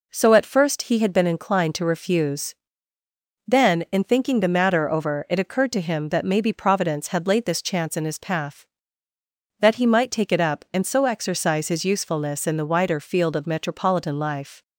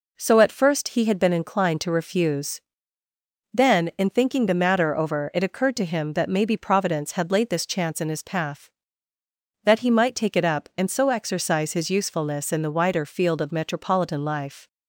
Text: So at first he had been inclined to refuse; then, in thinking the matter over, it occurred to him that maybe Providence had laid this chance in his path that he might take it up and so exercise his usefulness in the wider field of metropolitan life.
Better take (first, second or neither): neither